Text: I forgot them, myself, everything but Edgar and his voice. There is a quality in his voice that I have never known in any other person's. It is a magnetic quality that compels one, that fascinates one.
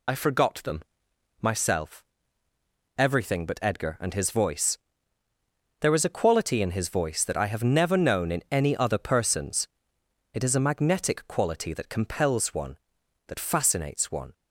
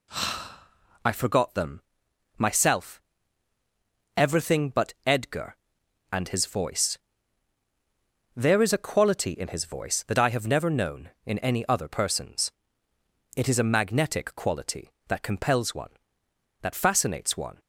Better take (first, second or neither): second